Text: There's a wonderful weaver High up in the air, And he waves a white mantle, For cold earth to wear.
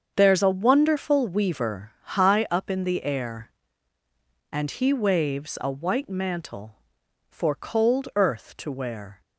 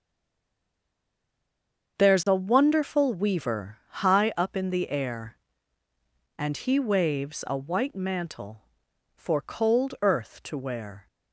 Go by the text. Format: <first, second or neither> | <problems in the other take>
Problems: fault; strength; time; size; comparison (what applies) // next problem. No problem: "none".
first | stays silent before the first word; noticeable; until 1.9 s; 1.9 s long // starts louder than the rest; until 3.0 s; 7 dB; also in the first